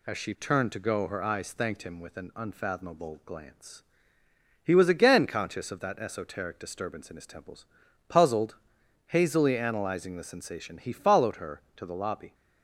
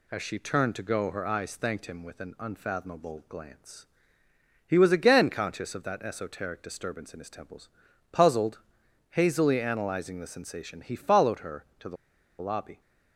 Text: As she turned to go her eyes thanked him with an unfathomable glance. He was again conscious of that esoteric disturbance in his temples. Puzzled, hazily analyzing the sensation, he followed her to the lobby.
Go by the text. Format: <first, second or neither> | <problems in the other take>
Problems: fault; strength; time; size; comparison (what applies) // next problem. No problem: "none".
first | pauses between "the" and "lobby"; at 11.9 s; 0.44 s long